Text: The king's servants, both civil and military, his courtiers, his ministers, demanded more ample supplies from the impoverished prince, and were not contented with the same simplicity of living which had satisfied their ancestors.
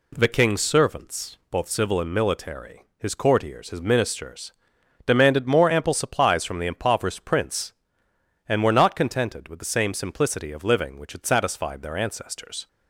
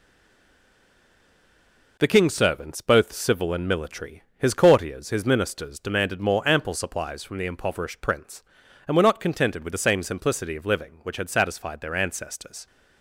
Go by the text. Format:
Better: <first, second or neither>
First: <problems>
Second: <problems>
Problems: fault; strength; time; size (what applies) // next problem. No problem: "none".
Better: first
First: none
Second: stays silent before the first word; noticeable; until 1.9 s; 1.9 s long